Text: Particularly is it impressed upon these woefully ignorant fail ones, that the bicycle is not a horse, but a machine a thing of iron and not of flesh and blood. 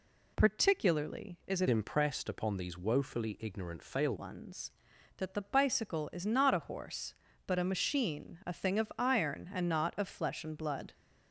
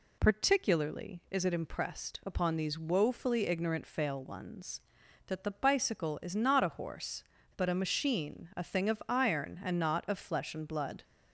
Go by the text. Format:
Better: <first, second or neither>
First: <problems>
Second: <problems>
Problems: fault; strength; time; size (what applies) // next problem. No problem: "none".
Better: second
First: changes voice from "impressed" to "fail"; from 1.6 to 4.1 s; 2.5 s long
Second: none